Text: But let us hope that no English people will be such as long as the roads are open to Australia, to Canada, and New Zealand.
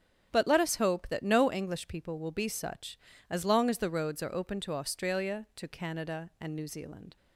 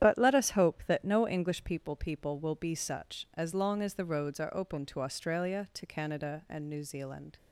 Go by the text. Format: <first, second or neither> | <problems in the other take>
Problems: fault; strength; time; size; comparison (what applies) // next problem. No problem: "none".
first | starts louder than the rest; strong; until 1.0 s; 10.5 dB; strong in the first // says "people" twice; at 1.9 s